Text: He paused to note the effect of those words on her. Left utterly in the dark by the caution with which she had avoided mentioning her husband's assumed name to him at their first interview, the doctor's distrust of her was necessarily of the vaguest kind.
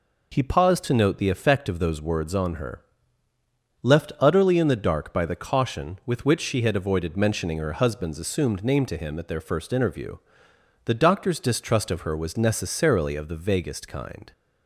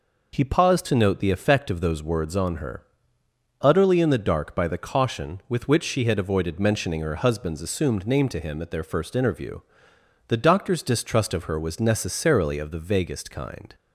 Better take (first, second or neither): first